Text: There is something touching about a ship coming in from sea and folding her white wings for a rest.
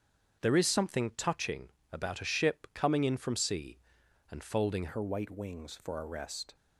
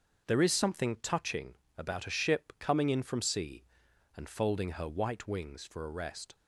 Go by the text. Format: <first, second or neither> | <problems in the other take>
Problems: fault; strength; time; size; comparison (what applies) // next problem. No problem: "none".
second | starts louder than the rest; strong; until 1.4 s; 7.5 dB; also in the second // pauses between "touching" and "about"; slight; at 1.6 s; 0.22 s long; slight in the second // changes voice at "her"; from 4.8 s on; 1.7 s long